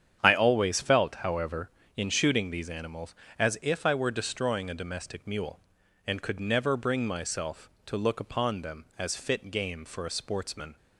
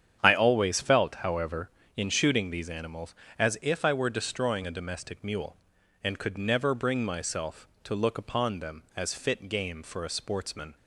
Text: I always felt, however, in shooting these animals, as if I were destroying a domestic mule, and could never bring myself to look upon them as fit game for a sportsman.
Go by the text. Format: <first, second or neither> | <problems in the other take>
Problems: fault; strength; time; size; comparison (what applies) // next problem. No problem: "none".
neither | starts louder than the rest; strong; the same in both